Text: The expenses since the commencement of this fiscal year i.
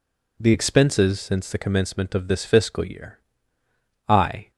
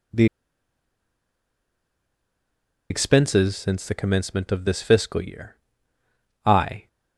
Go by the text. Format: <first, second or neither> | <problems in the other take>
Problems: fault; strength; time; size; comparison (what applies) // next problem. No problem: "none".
first | pauses between "The" and "expenses"; strong; at 0.2 s; 2.6 s long // pauses between "year" and "i"; noticeable; at 5.5 s; 0.86 s long; noticeable in the first